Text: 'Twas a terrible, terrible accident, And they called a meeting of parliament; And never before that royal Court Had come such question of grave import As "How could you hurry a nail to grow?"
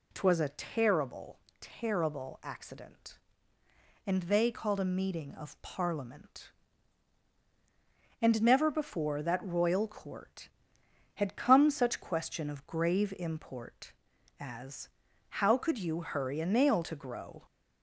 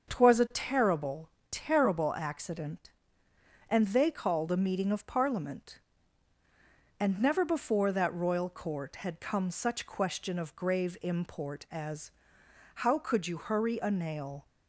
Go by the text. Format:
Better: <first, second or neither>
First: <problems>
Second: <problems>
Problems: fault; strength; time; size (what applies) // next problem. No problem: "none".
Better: first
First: pauses between "As" and "How"; at 14.8 s; 0.40 s long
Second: starts louder than the rest; until 1.1 s; 6.5 dB // pauses between "As" and "How"; noticeable; at 12.0 s; 0.64 s long // stops before "to grow"; at 14.4 s